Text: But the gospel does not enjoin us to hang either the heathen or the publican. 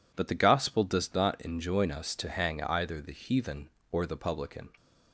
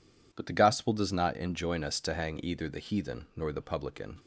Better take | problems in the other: first | says "nor" for "or"; at 3.3 s

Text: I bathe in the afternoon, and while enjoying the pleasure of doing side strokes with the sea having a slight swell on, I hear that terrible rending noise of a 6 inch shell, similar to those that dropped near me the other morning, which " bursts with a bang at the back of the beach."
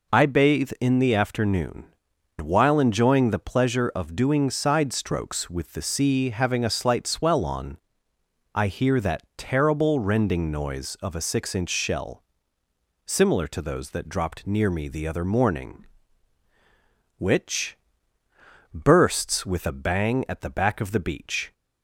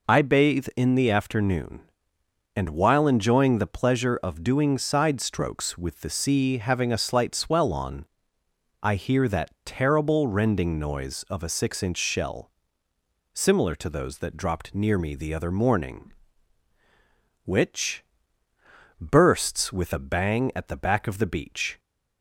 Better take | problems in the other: second | skips "and"; at 2.1 s

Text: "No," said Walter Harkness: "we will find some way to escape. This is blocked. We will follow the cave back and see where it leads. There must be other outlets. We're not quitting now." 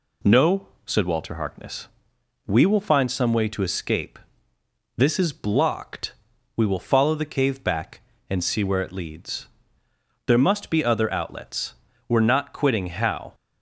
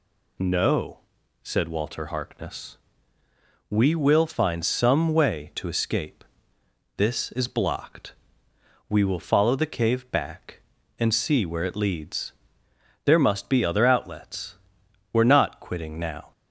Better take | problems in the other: second | says "how" for "now"; at 12.8 s

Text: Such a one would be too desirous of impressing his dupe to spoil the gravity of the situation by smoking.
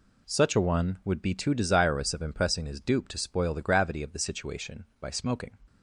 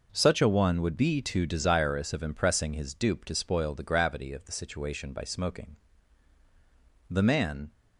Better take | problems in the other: first | goes on to say "The man"; noticeable; from 7.0 s on; 0.62 s long

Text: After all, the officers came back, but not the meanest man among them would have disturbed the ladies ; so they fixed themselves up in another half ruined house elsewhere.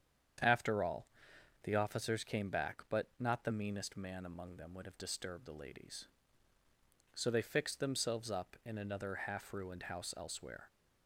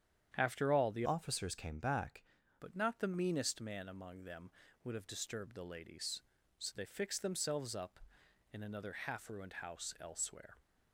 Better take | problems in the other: first | starts louder than the rest; strong; until 1.3 s; 9 dB; strong in the first // changes voice from "officers" to "back"; from 1.0 to 2.2 s; 1.2 s long

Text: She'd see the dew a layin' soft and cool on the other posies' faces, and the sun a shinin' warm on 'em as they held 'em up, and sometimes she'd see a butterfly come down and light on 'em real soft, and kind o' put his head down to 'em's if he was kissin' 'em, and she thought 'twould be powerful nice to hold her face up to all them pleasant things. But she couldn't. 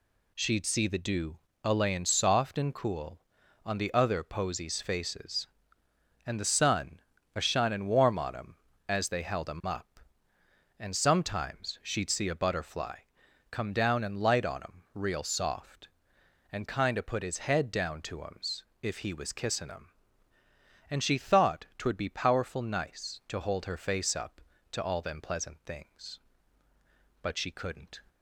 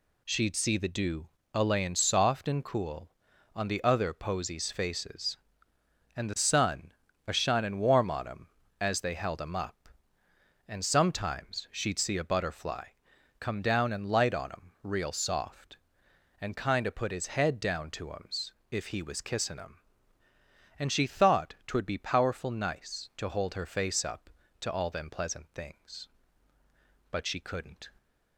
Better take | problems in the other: neither | pauses between "dew" and "a"; slight; the same in both // pauses between "sun" and "a"; slight; the same in both // pauses between "butterfly" and "come"; noticeable; the same in both // pauses between "em's" and "if"; slight; the same in both

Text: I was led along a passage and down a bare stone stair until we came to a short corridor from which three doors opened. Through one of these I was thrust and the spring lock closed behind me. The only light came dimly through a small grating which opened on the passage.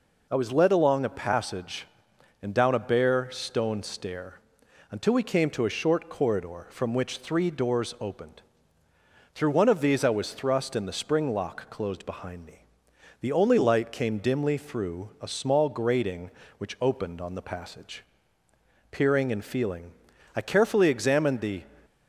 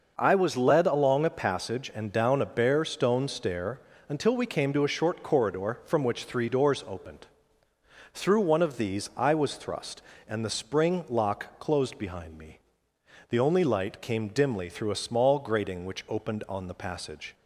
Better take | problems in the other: second | pauses between "stair" and "until"; noticeable; at 4.3 s; 0.50 s long; slight in the second // goes on to say "Peering and feeling I carefully examined the"; strong; from 18.9 s on; 2.7 s long

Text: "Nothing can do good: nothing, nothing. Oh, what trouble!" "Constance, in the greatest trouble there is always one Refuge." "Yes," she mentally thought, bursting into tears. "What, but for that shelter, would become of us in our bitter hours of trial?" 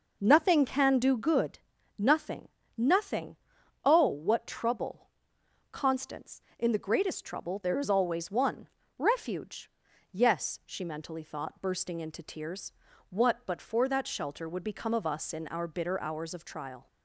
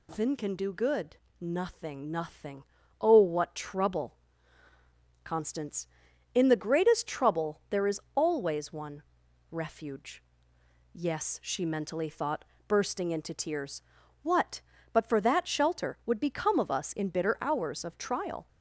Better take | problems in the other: first | pauses between "is" and "always"; slight; at 7.9 s; 0.16 s long // pauses between "one" and "Refuge"; noticeable; at 9.0 s; 0.48 s long; slight in the first // skips "our"; at 17.0 s

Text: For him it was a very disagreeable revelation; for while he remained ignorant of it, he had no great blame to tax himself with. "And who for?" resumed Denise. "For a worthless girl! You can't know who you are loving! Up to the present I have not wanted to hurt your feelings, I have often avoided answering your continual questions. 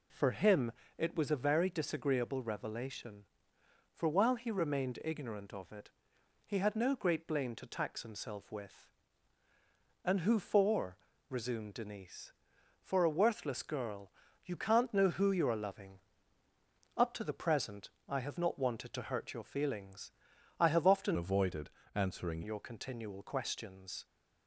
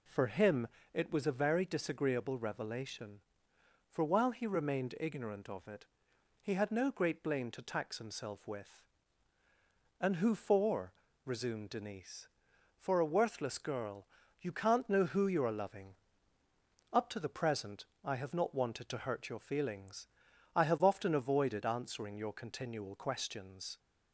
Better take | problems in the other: second | pauses between "him" and "it"; slight; at 0.7 s; 0.26 s long; slight in the second // pauses between "present" and "I"; slight; at 17.8 s; 0.20 s long; slight in the second // changes voice from "avoided" to "answering"; from 21.1 to 22.4 s; 1.3 s long // pauses between "avoided" and "answering"; slight; at 21.7 s; 0.24 s long

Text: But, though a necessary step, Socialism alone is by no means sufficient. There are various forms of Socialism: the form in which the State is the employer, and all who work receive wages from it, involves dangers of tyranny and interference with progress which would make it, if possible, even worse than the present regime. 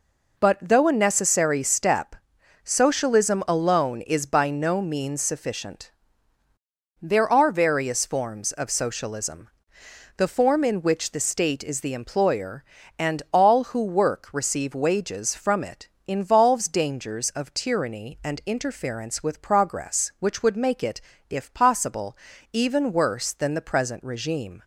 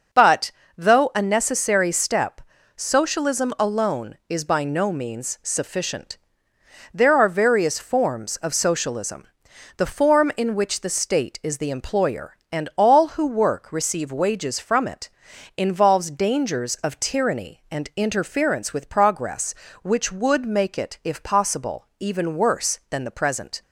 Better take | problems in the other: first | stops before "regime"; at 23.6 s

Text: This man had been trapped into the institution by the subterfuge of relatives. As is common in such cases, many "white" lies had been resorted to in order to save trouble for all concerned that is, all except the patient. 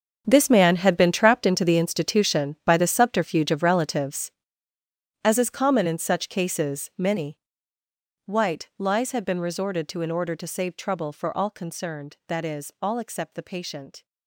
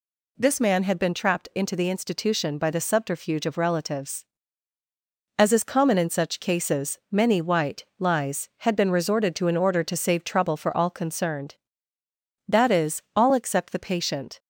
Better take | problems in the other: second | gets quieter; strong; throughout; 14.5 dB // pauses between "many" and "white"; noticeable; at 7.3 s; 0.86 s long

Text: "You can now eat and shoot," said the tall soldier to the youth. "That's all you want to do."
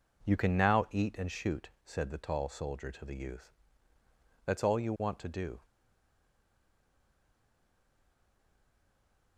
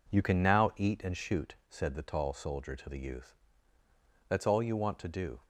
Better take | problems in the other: second | stays silent after the last word; strong; from 5.6 s on; 3.7 s long

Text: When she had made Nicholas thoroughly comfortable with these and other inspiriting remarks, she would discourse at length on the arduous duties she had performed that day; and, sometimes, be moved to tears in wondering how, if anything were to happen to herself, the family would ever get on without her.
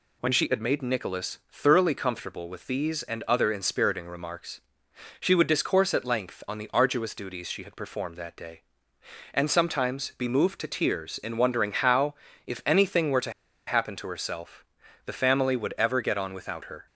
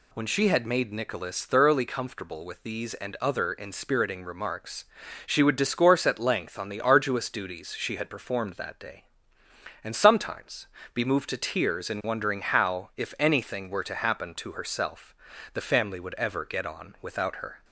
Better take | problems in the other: second | pauses between "to" and "happen"; slight; at 13.3 s; 0.35 s long

